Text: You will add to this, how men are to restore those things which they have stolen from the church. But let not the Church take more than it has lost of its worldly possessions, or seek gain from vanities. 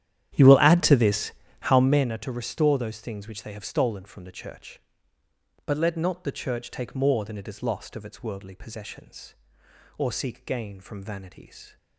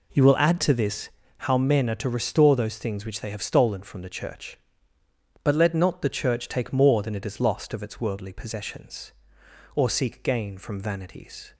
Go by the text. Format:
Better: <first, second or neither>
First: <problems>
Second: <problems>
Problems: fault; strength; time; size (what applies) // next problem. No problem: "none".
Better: second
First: starts louder than the rest; strong; until 2.2 s; 11 dB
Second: none